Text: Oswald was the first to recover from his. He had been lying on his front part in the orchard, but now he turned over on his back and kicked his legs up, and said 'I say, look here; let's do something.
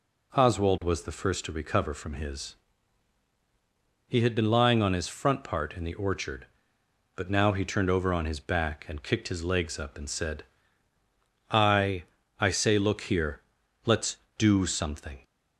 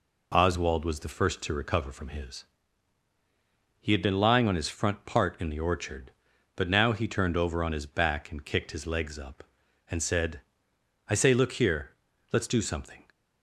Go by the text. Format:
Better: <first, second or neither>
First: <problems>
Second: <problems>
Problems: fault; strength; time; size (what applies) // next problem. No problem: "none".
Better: second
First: pauses between "said" and "I"; at 10.4 s; 1.0 s long // says "I" twice; at 12.4 s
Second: pauses between "said" and "I"; noticeable; at 10.4 s; 0.66 s long